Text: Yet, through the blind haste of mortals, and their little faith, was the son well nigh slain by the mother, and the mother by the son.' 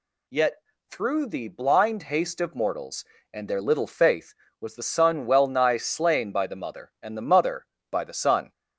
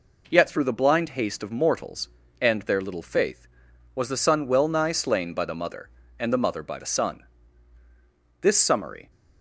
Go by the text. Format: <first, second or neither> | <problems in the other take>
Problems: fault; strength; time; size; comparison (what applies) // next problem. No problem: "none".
first | goes on to say "This summary"; noticeable; from 8.4 s on; 0.70 s long